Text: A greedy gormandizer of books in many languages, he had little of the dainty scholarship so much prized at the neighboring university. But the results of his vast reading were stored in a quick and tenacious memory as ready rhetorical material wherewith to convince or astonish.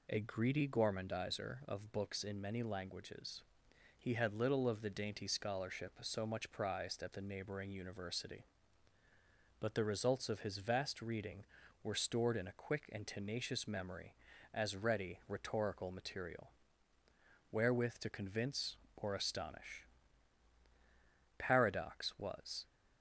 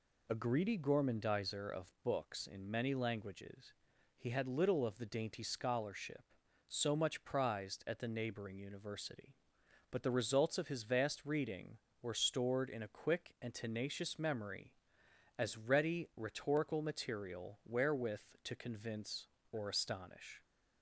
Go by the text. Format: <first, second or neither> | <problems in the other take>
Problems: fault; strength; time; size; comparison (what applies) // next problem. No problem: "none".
second | pauses between "material" and "wherewith"; at 16.5 s; 1.0 s long // goes on to say "Paradox was"; noticeable; from 21.3 s on; 1.2 s long